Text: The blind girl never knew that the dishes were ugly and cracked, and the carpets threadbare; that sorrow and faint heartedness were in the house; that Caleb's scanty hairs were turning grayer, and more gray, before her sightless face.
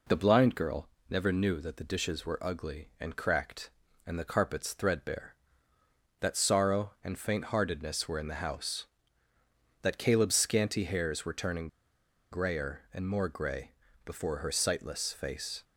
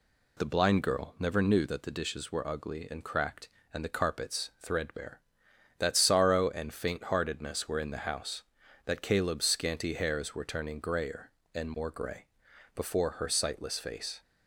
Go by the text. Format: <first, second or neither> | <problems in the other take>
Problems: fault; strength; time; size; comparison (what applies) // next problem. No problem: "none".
second | pauses between "girl" and "never"; slight; at 0.8 s; 0.22 s long // pauses between "turning" and "grayer"; noticeable; at 11.6 s; 0.63 s long